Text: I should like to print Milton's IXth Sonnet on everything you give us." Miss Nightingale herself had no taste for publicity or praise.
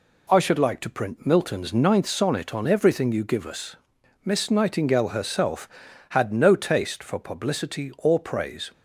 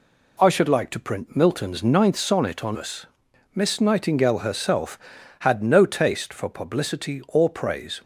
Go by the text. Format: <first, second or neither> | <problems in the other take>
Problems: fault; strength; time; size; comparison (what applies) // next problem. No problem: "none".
first | skips "everything you give"; at 2.7 s